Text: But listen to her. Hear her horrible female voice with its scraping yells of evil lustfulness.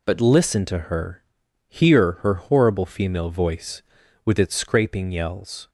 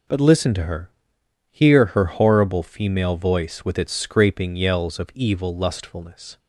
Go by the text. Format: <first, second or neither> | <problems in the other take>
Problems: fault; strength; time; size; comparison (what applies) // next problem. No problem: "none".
second | stops before "of evil lustfulness"; at 5.6 s